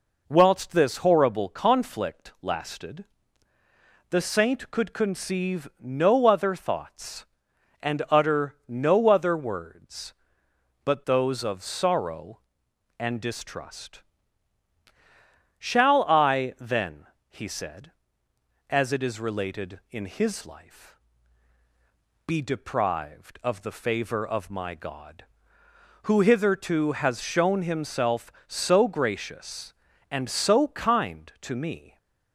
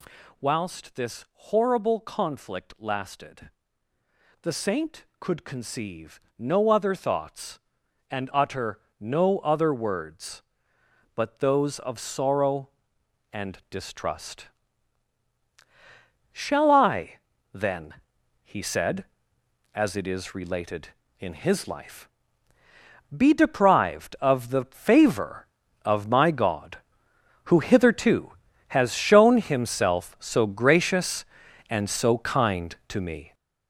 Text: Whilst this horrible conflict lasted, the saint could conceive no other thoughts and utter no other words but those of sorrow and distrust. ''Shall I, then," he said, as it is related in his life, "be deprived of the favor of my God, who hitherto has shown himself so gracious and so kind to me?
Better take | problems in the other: first | gets louder; strong; throughout; 8.5 dB // pauses between "conceive" and "no"; slight; at 6.1 s; 0.18 s long // pauses between "utter" and "no"; slight; at 8.7 s; 0.20 s long

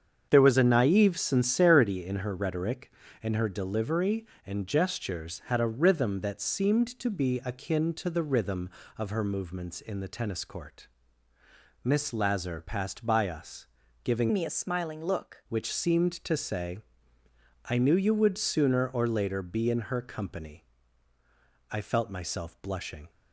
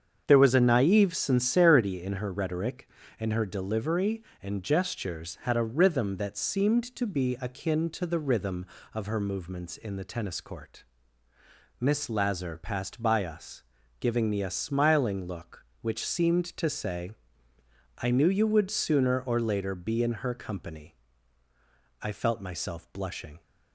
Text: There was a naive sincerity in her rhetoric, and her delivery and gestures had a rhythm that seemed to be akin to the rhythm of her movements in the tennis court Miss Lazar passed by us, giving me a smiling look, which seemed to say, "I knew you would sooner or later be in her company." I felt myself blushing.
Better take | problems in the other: second | starts louder than the rest; strong; until 1.3 s; 7.5 dB; strong in the second // pauses between "court" and "Miss"; noticeable; at 10.8 s; 0.96 s long; noticeable in the second // changes voice from "me" to "look"; from 14.3 to 15.4 s; 1.1 s long

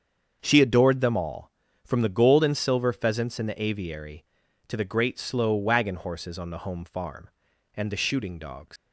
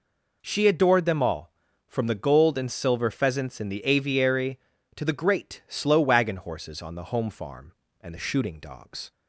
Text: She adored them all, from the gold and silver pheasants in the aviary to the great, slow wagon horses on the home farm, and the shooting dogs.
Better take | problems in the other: second | starts louder than the rest; strong; until 1.4 s; 7 dB // leaves "dogs" unfinished; at 8.7 s; 100 ms

